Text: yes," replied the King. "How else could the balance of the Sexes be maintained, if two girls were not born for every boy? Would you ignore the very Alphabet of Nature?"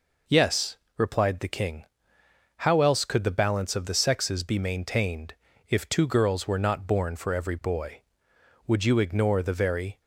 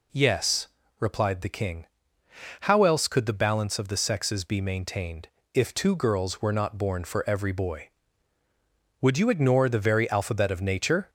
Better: second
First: stops before "Alphabet of Nature"; at 10.0 s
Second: none

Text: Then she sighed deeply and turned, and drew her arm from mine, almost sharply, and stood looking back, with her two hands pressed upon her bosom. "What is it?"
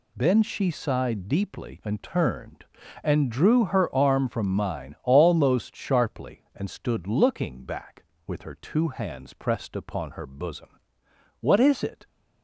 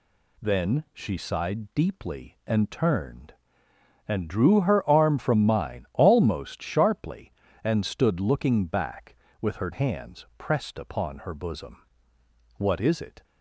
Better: first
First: none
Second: skips "two"; at 9.7 s

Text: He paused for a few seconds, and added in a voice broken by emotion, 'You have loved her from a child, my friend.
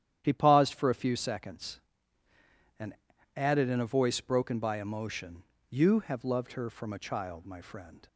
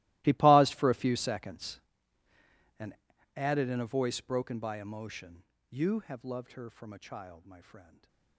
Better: first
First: starts louder than the rest; strong; until 1.2 s; 10.5 dB // pauses between "and" and "added"; at 2.9 s; 0.42 s long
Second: gets quieter; strong; throughout; 20 dB // starts louder than the rest; strong; until 1.2 s; 18 dB // pauses between "and" and "added"; at 2.9 s; 0.42 s long // stays silent after the last word; slight; from 7.8 s on; 0.5 s long

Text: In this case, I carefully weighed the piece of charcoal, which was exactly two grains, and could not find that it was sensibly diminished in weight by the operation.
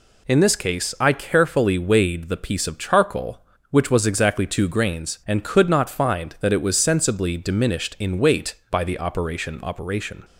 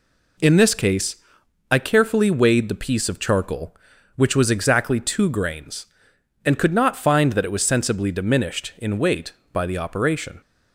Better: second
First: says "operation" twice; at 9.6 s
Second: none

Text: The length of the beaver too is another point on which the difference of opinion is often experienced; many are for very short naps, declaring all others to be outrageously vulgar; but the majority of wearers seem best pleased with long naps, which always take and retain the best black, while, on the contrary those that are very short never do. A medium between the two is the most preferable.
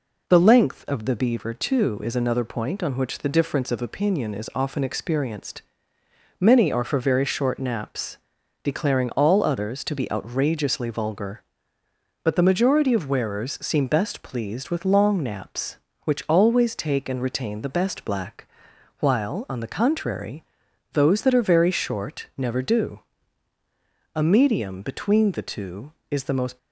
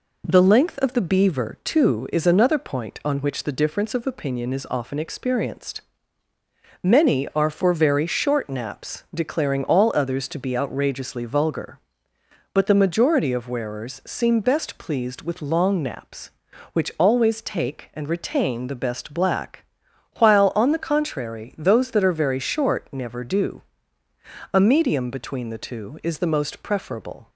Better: second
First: pauses between "contrary" and "those"; noticeable; at 20.4 s; 0.52 s long // stops before "preferable"; at 26.5 s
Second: none

